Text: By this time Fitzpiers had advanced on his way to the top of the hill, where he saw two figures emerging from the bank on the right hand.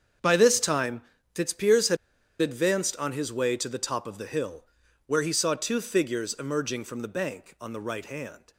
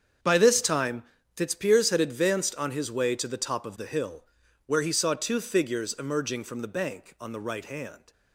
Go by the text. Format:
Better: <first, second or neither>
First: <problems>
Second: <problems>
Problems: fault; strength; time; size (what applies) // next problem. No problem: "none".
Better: second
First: starts louder than the rest; strong; until 1.5 s; 8 dB // pauses between "time" and "Fitzpiers"; slight; at 1.0 s; 0.32 s long // pauses between "had" and "advanced"; at 1.9 s; 0.45 s long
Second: starts louder than the rest; strong; until 1.5 s; 8 dB // pauses between "time" and "Fitzpiers"; slight; at 1.0 s; 0.32 s long